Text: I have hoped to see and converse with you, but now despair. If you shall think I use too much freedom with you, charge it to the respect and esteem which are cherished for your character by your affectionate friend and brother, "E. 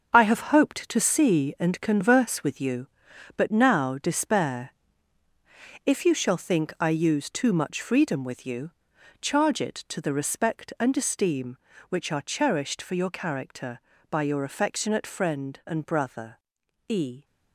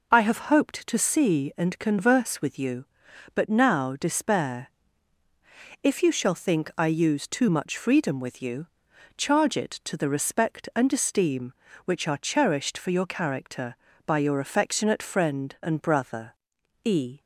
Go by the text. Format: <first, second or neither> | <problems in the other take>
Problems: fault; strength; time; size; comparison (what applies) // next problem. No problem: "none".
second | gets quieter; strong; throughout; 9 dB